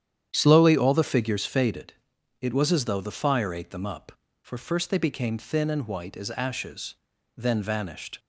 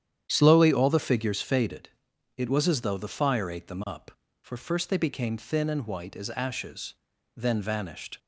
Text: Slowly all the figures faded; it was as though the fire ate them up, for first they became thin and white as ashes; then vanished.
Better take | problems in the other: neither | starts louder than the rest; strong; the same in both

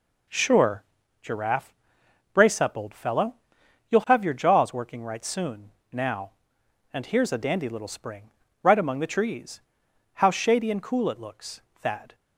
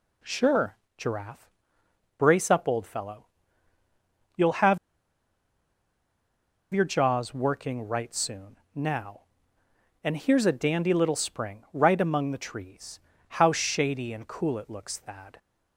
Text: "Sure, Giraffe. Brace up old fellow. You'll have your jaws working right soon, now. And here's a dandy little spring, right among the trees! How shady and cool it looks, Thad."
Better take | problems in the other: first | pauses between "have" and "your"; strong; at 4.7 s; 1.9 s long

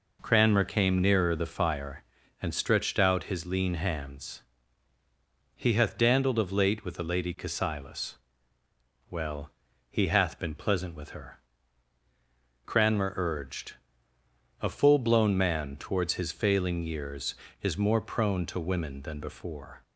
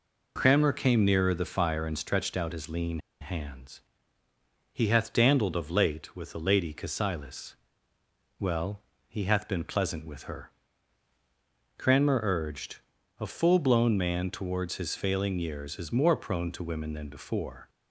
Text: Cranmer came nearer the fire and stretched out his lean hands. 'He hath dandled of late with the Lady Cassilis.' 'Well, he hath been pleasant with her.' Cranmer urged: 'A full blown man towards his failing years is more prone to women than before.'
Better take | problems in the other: first | pauses between "lean" and "hands"; slight; at 2.9 s; 0.22 s long

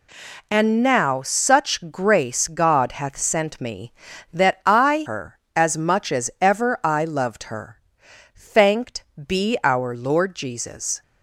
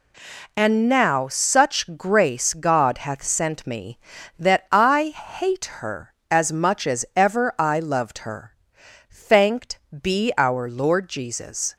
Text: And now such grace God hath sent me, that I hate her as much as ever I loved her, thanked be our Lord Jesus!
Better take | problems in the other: second | skips "hate"; at 5.0 s // pauses between "thanked" and "be"; slight; at 9.0 s; 0.22 s long; slight in the second

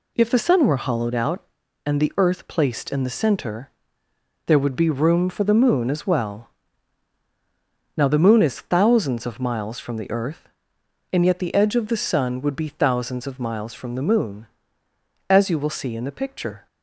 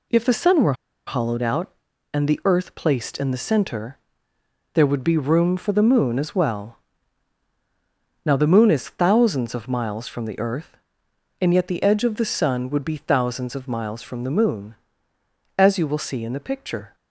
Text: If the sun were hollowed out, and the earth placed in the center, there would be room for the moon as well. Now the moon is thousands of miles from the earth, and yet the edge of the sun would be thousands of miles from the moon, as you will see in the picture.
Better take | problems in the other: first | pauses between "were" and "hollowed"; slight; at 0.7 s; 0.33 s long

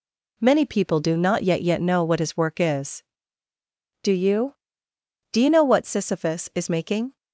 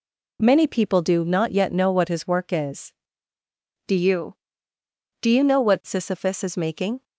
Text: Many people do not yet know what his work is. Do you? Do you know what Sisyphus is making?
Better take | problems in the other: second | says "yet" twice; at 1.6 s

